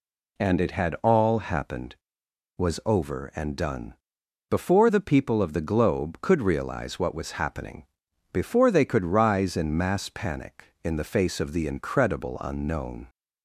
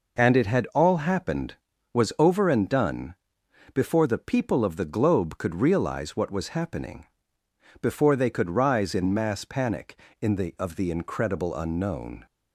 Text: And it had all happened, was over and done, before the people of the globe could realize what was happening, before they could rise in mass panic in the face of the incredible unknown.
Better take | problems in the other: first | skips "face"; at 10.5 s

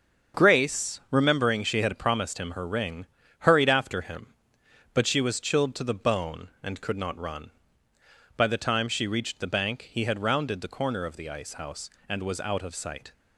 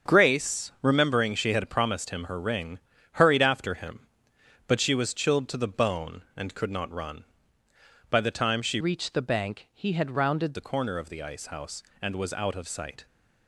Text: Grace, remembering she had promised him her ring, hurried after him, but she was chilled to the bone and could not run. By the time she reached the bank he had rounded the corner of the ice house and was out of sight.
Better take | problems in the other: first | starts louder than the rest; until 1.1 s; 7 dB; also in the first // changes voice from "reached" to "rounded"; from 8.8 to 10.5 s; 1.7 s long

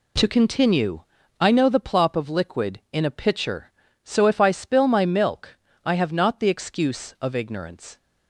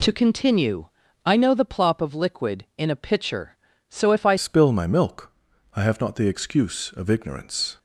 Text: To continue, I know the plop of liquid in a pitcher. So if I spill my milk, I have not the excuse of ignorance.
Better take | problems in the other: first | changes voice at "spill"; from 4.3 s on; 3.4 s long

